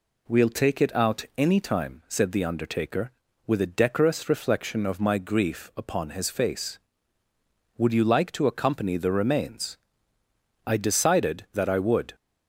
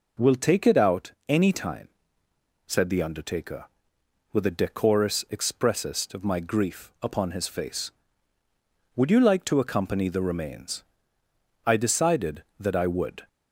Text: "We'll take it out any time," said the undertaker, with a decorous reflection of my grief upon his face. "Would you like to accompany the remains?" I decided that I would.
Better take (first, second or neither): first